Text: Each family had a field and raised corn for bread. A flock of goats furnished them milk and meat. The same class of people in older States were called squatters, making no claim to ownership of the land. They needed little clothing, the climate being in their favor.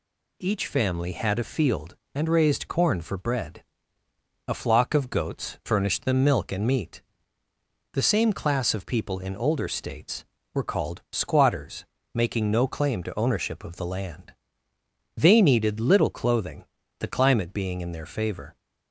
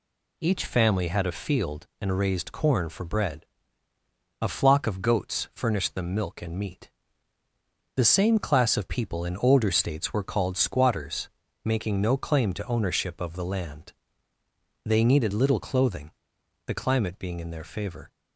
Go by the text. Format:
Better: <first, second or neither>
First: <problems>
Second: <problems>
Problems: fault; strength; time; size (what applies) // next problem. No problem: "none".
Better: neither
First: none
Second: none